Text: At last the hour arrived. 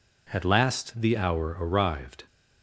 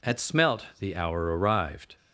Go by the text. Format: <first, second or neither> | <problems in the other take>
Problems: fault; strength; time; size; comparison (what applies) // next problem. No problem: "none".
first | says "smelt" for "last"; at 0.1 s